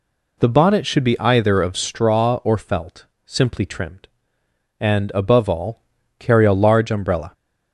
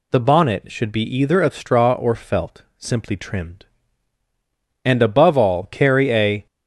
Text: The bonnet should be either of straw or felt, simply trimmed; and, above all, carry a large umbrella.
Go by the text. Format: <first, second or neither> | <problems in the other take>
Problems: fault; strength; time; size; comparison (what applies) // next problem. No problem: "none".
first | stops before "large umbrella"; at 6.4 s